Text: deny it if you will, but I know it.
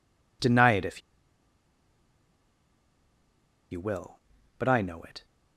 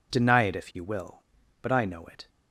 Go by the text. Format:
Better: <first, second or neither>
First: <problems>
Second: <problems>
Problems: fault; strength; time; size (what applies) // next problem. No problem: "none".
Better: second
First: pauses between "if" and "you"; strong; at 1.0 s; 2.7 s long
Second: none